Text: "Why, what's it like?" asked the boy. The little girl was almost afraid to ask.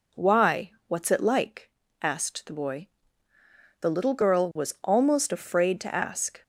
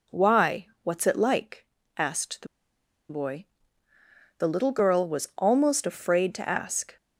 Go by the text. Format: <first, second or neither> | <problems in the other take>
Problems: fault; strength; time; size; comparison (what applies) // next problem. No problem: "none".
first | pauses between "the" and "boy"; noticeable; at 2.4 s; 0.63 s long